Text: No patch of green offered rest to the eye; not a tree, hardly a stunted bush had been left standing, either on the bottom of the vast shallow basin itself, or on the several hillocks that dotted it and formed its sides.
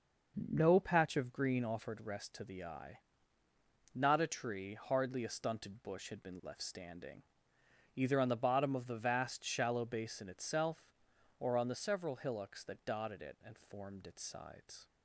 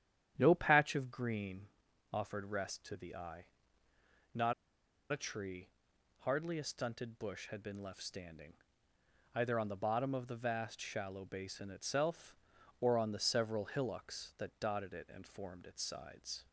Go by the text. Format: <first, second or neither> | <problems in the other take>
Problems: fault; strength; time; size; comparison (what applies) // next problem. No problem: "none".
first | starts louder than the rest; strong; until 1.3 s; 10 dB // pauses between "green" and "offered"; noticeable; at 1.6 s; 0.50 s long // pauses between "not" and "a"; noticeable; at 4.5 s; 0.57 s long